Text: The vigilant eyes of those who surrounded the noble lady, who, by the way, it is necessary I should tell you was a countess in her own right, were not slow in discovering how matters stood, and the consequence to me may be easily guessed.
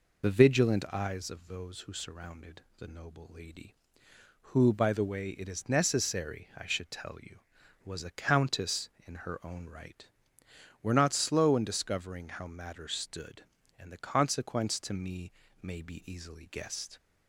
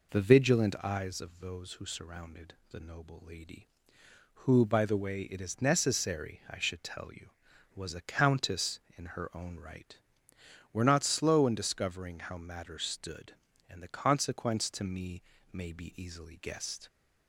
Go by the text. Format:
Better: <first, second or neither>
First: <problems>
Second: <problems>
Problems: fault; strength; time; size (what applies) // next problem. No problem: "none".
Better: second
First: loses the start of "The"; at 0.2 s; 30 ms // pauses between "surrounded" and "the"; slight; at 2.6 s; 0.16 s long // pauses between "me" and "may"; slight; at 15.3 s; 0.28 s long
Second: pauses between "surrounded" and "the"; slight; at 2.5 s; 0.16 s long // pauses between "me" and "may"; slight; at 15.2 s; 0.28 s long